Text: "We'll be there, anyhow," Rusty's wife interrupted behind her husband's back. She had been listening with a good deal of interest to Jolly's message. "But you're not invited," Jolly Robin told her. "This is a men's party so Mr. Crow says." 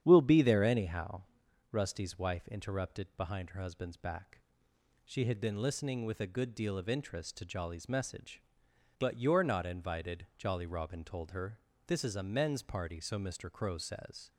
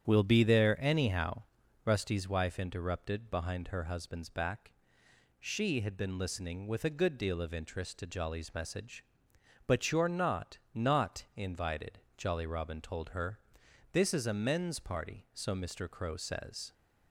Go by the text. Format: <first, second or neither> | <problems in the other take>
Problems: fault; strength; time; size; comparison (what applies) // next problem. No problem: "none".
first | starts louder than the rest; strong; until 1.0 s; 8.5 dB; strong in the first // says "not" twice; at 10.7 s